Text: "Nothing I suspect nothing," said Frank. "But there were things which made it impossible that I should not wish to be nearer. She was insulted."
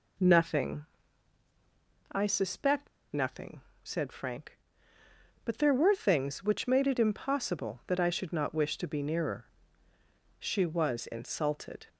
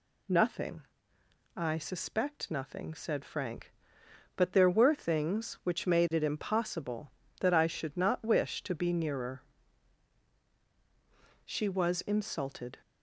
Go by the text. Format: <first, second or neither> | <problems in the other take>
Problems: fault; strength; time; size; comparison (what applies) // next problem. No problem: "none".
second | pauses between "Nothing" and "I"; strong; at 0.8 s; 1.2 s long; noticeable in the second // pauses between "suspect" and "nothing"; slight; at 2.8 s; 0.23 s long